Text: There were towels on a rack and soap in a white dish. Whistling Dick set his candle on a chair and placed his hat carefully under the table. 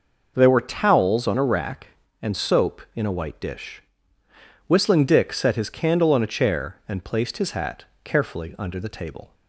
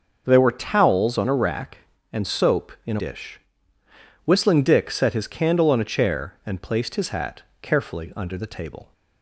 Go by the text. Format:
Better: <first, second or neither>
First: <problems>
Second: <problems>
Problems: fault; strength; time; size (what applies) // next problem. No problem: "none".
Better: first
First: pauses between "hat" and "carefully"; slight; at 7.8 s; 0.18 s long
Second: starts louder than the rest; noticeable; until 1.2 s; 6 dB // skips "white"; at 2.9 s // pauses between "hat" and "carefully"; slight; at 7.4 s; 0.18 s long